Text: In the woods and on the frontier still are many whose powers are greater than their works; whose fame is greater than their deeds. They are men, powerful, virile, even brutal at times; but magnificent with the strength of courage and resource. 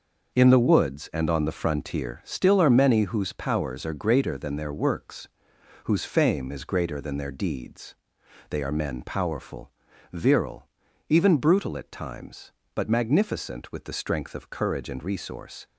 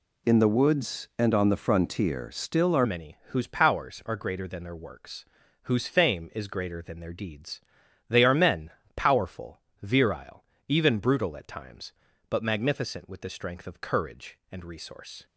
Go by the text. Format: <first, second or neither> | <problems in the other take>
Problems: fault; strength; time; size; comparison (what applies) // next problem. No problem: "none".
first | changes voice at "many"; from 2.8 s on; 12.4 s long